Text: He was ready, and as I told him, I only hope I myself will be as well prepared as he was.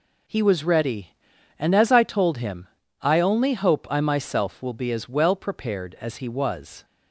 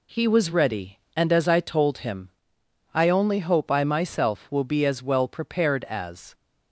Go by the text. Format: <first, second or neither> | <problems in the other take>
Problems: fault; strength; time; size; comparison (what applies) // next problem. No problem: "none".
first | stops before "he was"; at 6.3 s